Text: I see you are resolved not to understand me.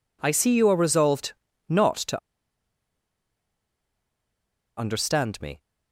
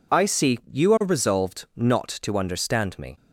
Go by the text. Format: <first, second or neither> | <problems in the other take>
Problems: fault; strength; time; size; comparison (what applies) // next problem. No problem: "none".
second | pauses between "resolved" and "not"; slight; at 1.3 s; 0.36 s long // pauses between "to" and "understand"; strong; at 2.1 s; 2.5 s long